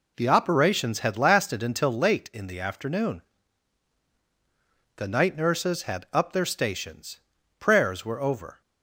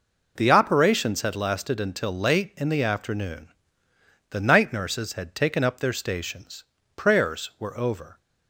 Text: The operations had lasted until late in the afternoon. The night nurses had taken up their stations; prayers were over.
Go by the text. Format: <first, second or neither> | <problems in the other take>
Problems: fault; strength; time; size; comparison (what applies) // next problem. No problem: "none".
second | skips "taken"; at 6.0 s